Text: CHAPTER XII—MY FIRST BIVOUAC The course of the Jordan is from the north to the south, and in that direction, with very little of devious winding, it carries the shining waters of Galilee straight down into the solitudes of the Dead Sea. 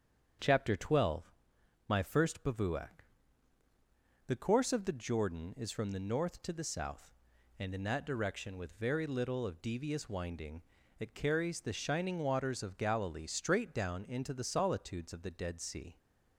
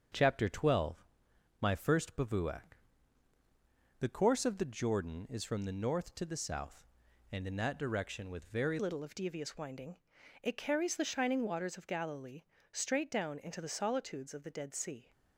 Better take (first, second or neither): first